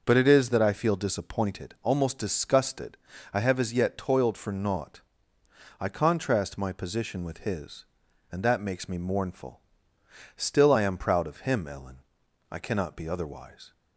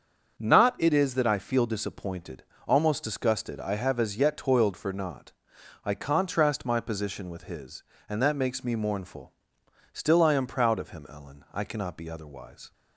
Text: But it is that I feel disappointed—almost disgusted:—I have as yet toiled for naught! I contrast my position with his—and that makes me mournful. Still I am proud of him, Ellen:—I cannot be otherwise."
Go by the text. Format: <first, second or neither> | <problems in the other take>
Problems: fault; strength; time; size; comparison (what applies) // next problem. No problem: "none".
first | starts louder than the rest; until 1.4 s; 7 dB // says "Not" for "But"; at 0.3 s